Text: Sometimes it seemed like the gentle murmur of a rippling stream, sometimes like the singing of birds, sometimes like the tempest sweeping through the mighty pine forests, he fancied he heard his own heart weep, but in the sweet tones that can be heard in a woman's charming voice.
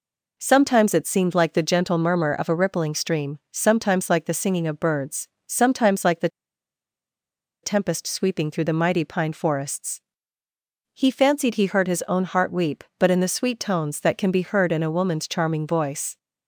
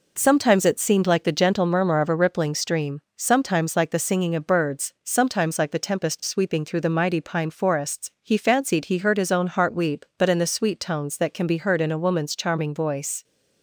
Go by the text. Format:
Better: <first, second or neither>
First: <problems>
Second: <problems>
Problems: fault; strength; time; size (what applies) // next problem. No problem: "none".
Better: second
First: pauses between "the" and "tempest"; strong; at 6.2 s; 1.3 s long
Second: none